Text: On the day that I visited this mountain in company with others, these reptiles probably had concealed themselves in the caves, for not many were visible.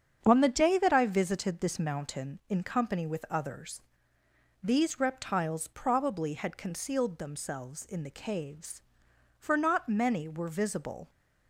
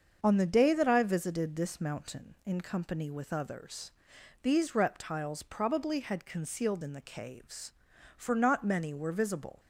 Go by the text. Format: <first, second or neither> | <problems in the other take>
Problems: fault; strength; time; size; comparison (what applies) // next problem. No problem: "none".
first | starts louder than the rest; until 1.2 s; 6.5 dB; strong in the first // skips "themselves"; at 6.8 s